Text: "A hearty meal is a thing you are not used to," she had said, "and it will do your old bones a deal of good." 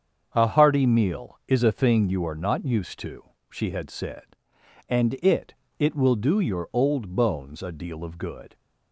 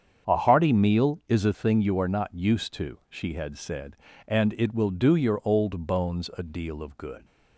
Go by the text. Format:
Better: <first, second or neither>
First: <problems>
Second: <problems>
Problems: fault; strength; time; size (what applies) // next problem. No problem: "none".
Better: second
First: starts louder than the rest; strong; until 1.3 s; 7 dB // says "it" twice; at 5.7 s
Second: starts louder than the rest; strong; until 1.3 s; 7.5 dB